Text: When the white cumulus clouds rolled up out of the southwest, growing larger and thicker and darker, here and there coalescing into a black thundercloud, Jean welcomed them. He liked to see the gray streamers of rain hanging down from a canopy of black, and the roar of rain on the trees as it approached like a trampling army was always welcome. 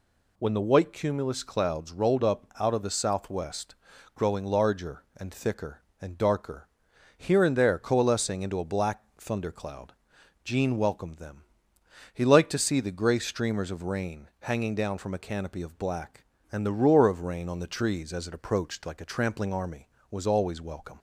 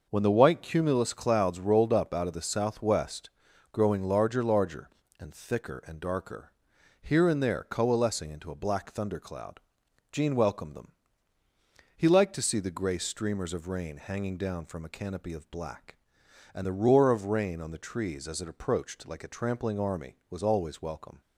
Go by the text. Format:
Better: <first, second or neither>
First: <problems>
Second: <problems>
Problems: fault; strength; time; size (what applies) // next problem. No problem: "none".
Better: first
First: none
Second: says "larger" twice; at 4.4 s